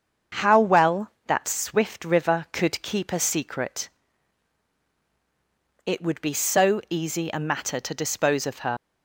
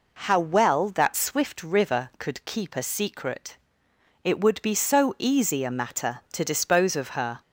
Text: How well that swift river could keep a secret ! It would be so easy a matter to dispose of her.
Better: second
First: starts louder than the rest; until 1.5 s; 7 dB // leaves "her" unfinished; at 8.7 s; 80 ms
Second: none

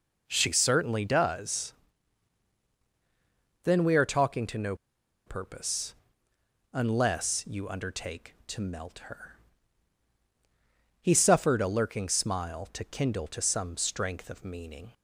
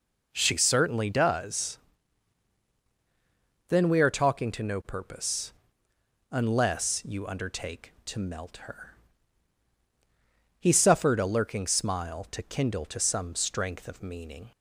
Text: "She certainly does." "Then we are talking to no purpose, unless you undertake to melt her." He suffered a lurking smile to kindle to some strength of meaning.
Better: second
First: pauses between "no" and "purpose"; noticeable; at 4.7 s; 0.51 s long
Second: none

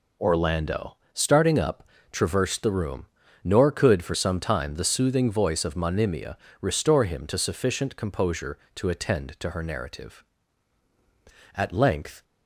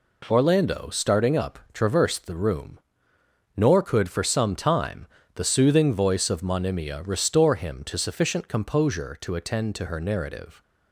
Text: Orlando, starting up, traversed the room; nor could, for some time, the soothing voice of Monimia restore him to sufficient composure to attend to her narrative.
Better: second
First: pauses between "Monimia" and "restore"; slight; at 6.3 s; 0.24 s long // goes on to say "At length"; noticeable; from 11.5 s on; 0.68 s long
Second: none

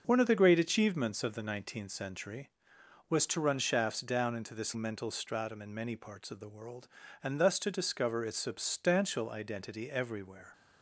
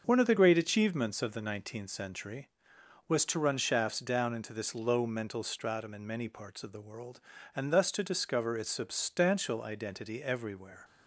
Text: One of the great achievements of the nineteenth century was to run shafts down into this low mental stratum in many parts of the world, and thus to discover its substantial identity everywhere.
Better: second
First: starts louder than the rest; noticeable; until 1.0 s; 6 dB // skips "low"; at 4.7 s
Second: starts louder than the rest; until 1.0 s; 6.5 dB

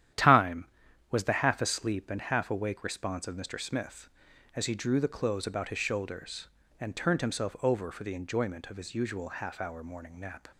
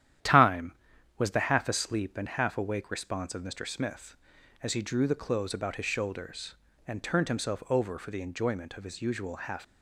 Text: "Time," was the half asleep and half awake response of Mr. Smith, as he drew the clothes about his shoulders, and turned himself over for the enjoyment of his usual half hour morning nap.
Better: first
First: starts louder than the rest; strong; until 1.5 s; 11 dB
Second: starts louder than the rest; strong; until 1.6 s; 11 dB // stops before "hour morning nap"; at 9.6 s

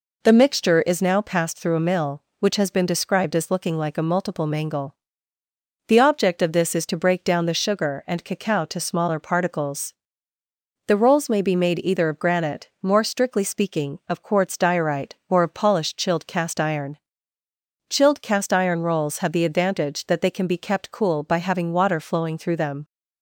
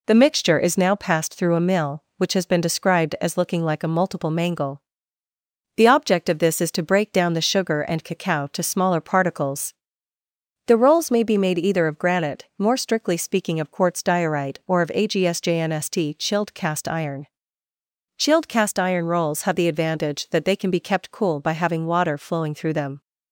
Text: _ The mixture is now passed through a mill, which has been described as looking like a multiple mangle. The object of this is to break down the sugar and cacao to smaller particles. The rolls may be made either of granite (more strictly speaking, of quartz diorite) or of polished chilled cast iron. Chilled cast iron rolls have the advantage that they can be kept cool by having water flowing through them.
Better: first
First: none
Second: says "agsjnst" for "polished"; at 14.9 s

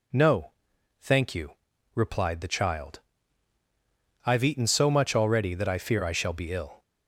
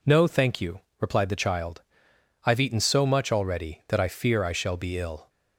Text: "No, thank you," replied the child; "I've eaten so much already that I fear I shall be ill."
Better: neither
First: none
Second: none

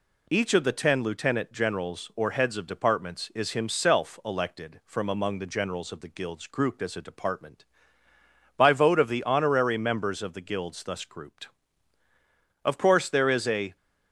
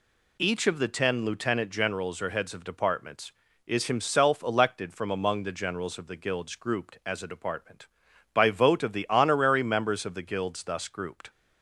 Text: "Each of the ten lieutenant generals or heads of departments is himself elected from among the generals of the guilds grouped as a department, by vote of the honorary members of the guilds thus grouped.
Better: second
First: goes on to say "Of course there is a"; noticeable; from 12.6 s on; 1.1 s long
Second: none

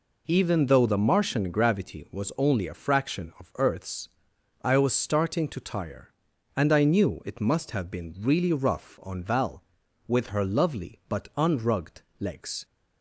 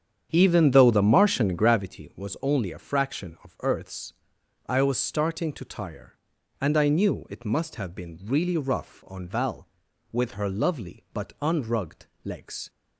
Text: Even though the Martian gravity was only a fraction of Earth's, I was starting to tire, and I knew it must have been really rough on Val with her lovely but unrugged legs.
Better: first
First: pauses between "unrugged" and "legs"; slight; at 12.0 s; 0.18 s long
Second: starts louder than the rest; strong; until 1.9 s; 8 dB // pauses between "unrugged" and "legs"; slight; at 12.0 s; 0.18 s long

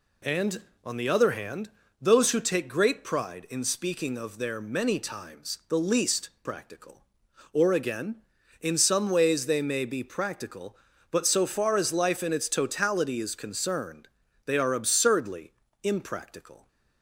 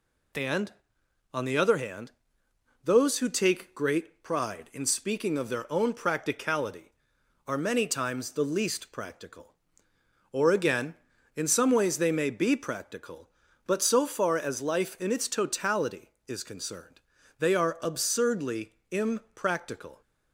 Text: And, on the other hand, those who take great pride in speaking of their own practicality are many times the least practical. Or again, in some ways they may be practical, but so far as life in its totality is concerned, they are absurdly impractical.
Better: second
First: skips "own practicality are"; at 4.5 s // pauses between "absurdly" and "impractical"; slight; at 15.5 s; 0.32 s long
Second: pauses between "absurdly" and "impractical"; slight; at 18.7 s; 0.16 s long

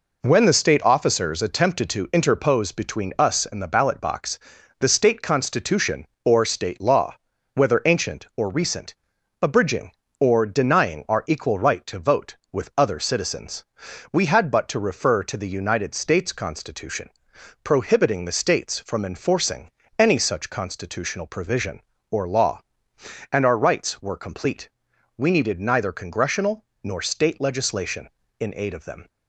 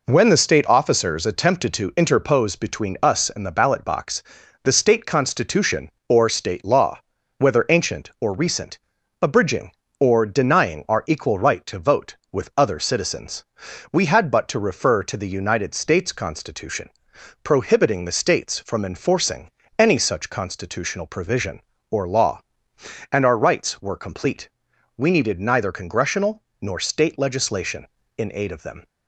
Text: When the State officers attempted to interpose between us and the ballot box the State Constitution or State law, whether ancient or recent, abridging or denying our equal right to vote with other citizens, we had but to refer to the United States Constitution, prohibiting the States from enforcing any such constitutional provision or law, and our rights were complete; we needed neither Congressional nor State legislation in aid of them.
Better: neither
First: pauses between "box" and "the"; at 4.3 s; 0.40 s long // pauses between "enforcing" and "any"; slight; at 19.7 s; 0.28 s long // pauses between "Congressional" and "nor"; slight; at 26.6 s; 0.18 s long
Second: pauses between "box" and "the"; at 4.2 s; 0.40 s long // pauses between "enforcing" and "any"; slight; at 19.5 s; 0.28 s long // pauses between "Congressional" and "nor"; slight; at 26.4 s; 0.18 s long

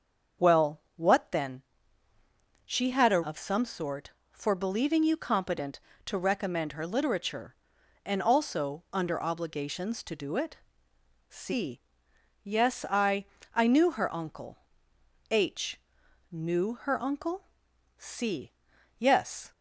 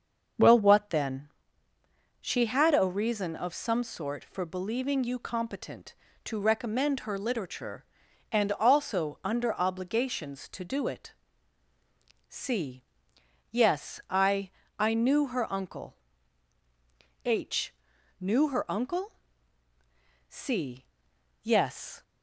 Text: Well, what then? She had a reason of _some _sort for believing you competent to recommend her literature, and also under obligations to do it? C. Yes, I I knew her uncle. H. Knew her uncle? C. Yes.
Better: second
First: starts louder than the rest; until 1.5 s; 6.5 dB // skips "reason"; at 3.2 s // pauses between "I" and "I"; slight; at 13.2 s; 0.28 s long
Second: starts louder than the rest; until 2.3 s; 6.5 dB // pauses between "I" and "I"; slight; at 14.5 s; 0.28 s long

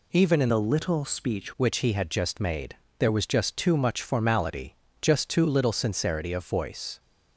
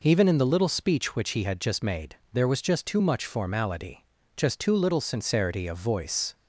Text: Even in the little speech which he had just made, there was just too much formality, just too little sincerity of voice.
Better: second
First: changes voice from "the" to "speech"; from 0.4 to 1.5 s; 1.1 s long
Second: none

